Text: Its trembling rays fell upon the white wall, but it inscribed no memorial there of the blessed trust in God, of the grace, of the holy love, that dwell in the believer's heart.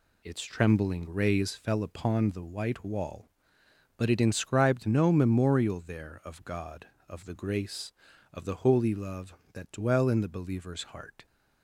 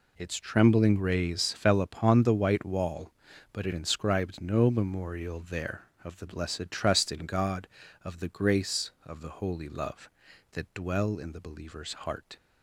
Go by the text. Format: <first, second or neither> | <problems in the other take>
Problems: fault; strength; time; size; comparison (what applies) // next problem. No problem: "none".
second | skips "the blessed trust in"; at 6.4 s